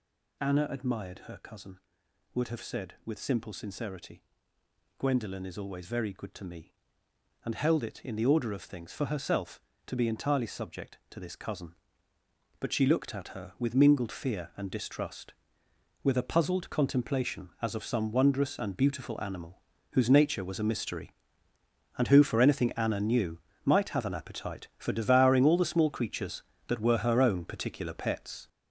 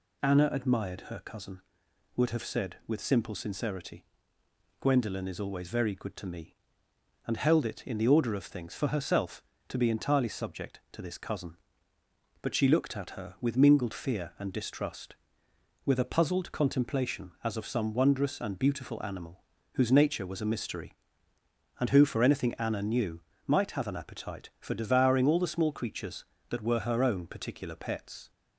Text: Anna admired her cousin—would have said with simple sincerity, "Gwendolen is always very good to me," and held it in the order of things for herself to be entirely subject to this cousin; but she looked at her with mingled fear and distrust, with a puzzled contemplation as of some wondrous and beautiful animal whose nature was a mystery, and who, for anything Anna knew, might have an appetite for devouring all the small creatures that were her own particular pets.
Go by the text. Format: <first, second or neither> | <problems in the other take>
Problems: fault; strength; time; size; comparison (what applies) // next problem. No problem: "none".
second | gets louder; throughout; 6.5 dB // pauses between "animal" and "whose"; slight; at 19.6 s; 0.30 s long; slight in the second